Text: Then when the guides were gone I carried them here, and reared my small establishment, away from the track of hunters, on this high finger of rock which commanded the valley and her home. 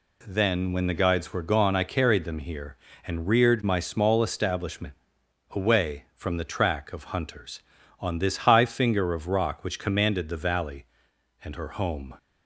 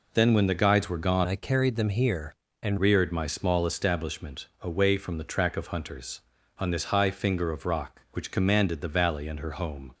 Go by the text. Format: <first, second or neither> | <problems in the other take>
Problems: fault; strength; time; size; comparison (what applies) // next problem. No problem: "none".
first | changes voice from "I" to "and"; from 1.2 to 2.7 s; 1.5 s long